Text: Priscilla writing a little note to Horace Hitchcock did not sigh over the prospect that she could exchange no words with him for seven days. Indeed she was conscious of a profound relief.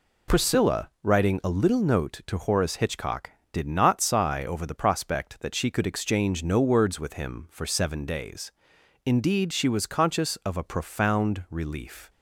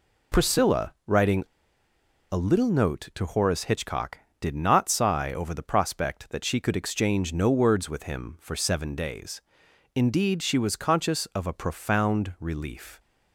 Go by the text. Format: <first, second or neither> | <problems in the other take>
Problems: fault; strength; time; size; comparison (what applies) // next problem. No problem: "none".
first | pauses between "writing" and "a"; noticeable; at 1.4 s; 0.84 s long